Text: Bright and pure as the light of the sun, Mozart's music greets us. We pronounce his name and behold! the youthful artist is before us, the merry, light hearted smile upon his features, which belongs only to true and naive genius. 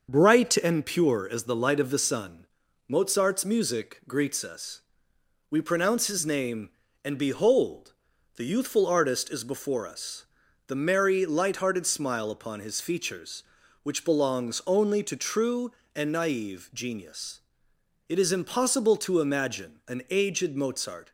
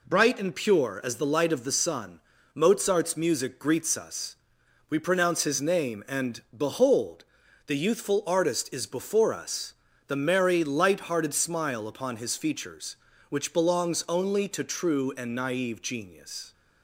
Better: second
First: starts louder than the rest; until 1.1 s; 6 dB // goes on to say "It is impossible to imagine an aged Mozart"; strong; from 18.0 s on; 3.0 s long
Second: none

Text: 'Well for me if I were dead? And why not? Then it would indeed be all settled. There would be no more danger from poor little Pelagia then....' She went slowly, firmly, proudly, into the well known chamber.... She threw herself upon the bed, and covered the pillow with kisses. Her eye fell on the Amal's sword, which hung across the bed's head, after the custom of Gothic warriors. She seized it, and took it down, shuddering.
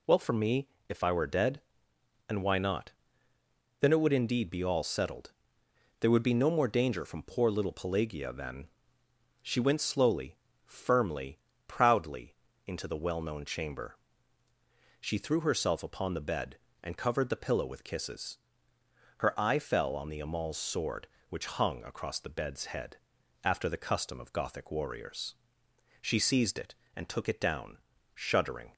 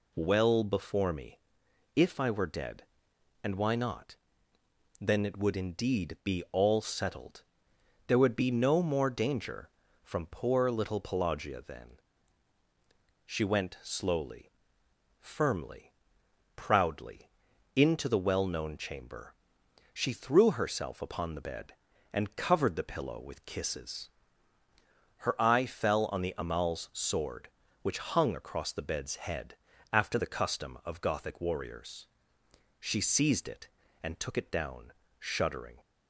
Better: first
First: pauses between "me" and "if"; slight; at 0.6 s; 0.20 s long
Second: says "before" for "for"; at 0.6 s // pauses between "me" and "if"; noticeable; at 1.3 s; 0.56 s long

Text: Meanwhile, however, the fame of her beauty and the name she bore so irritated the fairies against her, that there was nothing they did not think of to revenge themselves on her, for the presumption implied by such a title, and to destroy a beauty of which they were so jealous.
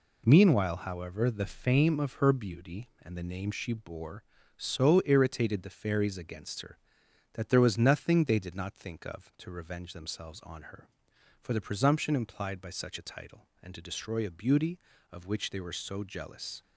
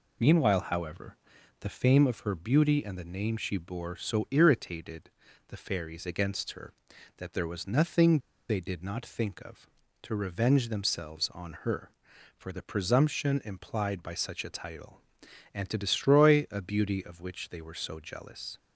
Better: first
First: none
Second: pauses between "irritated" and "the"; at 5.0 s; 0.38 s long // pauses between "nothing" and "they"; slight; at 8.1 s; 0.29 s long

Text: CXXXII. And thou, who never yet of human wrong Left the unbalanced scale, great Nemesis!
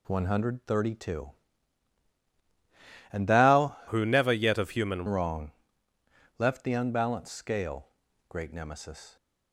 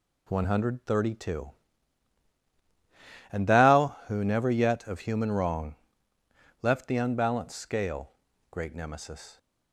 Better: second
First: changes voice from "who" to "human"; from 3.8 to 5.0 s; 1.2 s long // pauses between "wrong" and "Left"; noticeable; at 5.5 s; 0.86 s long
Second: pauses between "wrong" and "Left"; noticeable; at 5.7 s; 0.86 s long

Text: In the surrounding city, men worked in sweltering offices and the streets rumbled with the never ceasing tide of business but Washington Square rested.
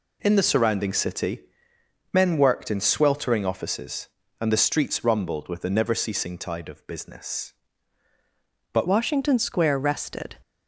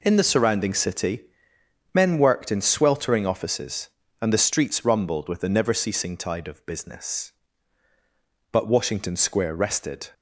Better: second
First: changes voice at "Washington"; from 8.8 s on; 1.5 s long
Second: none

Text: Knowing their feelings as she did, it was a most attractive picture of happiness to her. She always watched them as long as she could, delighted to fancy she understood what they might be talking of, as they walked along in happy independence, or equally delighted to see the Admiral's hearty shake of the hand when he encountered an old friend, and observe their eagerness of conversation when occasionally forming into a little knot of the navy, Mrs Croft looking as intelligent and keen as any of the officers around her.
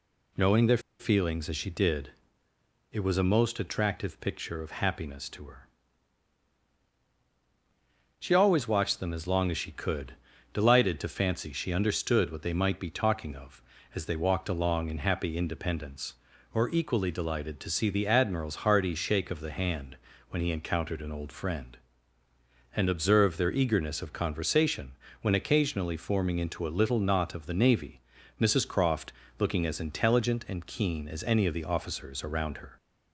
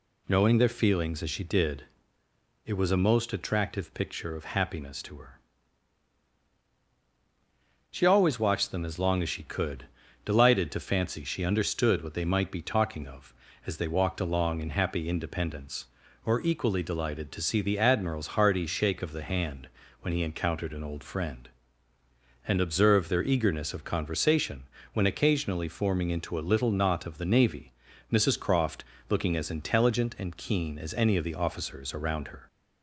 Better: second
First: pauses between "their" and "feelings"; slight; at 0.7 s; 0.20 s long // pauses between "hand" and "when"; slight; at 19.9 s; 0.36 s long // pauses between "conversation" and "when"; slight; at 24.9 s; 0.30 s long // pauses between "Croft" and "looking"; slight; at 29.1 s; 0.26 s long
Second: pauses between "hand" and "when"; slight; at 19.6 s; 0.36 s long // pauses between "conversation" and "when"; slight; at 24.6 s; 0.30 s long // pauses between "Croft" and "looking"; slight; at 28.8 s; 0.24 s long

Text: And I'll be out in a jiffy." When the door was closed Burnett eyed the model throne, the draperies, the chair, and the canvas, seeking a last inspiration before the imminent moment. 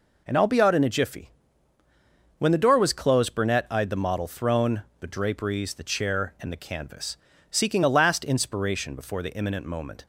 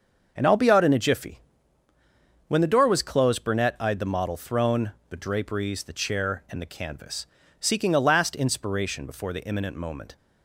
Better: first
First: none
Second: starts louder than the rest; until 1.7 s; 6.5 dB

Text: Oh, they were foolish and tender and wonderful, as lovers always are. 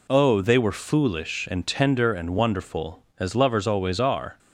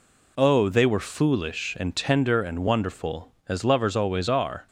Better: neither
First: none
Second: none

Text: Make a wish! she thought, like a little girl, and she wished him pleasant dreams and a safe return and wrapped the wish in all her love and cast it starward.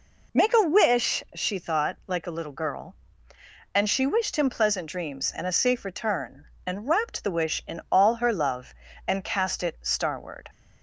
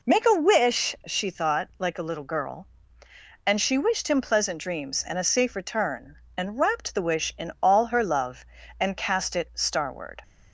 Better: neither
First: none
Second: none

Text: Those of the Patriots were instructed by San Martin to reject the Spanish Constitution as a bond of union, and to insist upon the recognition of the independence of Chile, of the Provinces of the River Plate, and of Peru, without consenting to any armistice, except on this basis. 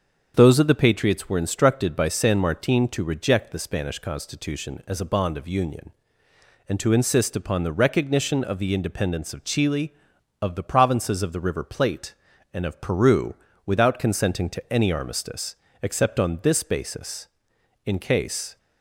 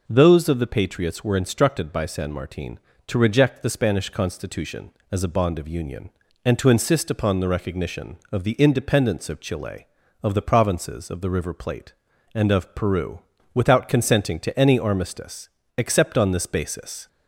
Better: second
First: starts louder than the rest; until 1.3 s; 7 dB // goes on to say "In case"; noticeable; from 17.8 s on; 0.72 s long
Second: none

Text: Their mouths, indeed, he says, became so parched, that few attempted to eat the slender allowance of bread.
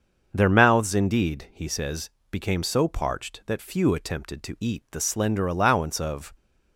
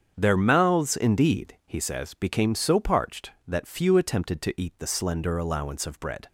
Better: second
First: starts louder than the rest; until 1.3 s; 6.5 dB // stops before "bread"; at 6.3 s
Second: starts louder than the rest; strong; until 1.1 s; 7.5 dB

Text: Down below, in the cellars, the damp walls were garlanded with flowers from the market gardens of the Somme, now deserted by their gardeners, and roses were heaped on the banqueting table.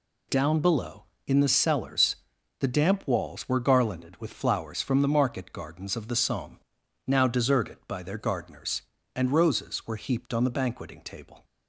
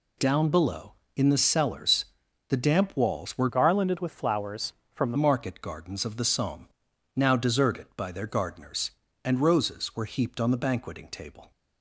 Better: first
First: none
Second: changes voice from "garlanded" to "the"; from 3.4 to 5.1 s; 1.7 s long

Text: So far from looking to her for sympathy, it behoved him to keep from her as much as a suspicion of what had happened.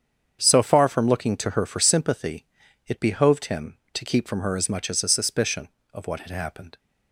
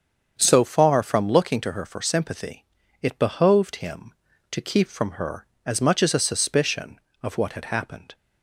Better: neither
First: starts louder than the rest; strong; until 1.4 s; 7.5 dB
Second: starts louder than the rest; strong; until 1.3 s; 7.5 dB

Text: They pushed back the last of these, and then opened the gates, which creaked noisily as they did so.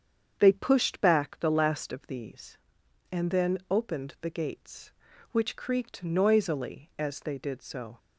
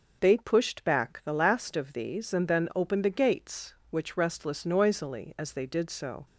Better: first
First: starts louder than the rest; strong; until 1.4 s; 7.5 dB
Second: starts louder than the rest; noticeable; until 1.2 s; 6 dB // says "restless" for "creaked"; at 4.1 s

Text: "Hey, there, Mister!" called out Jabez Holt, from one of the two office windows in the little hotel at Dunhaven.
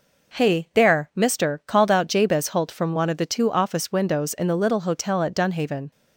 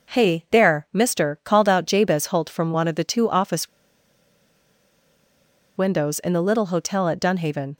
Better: first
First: none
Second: pauses between "office" and "windows"; strong; at 3.6 s; 2.0 s long

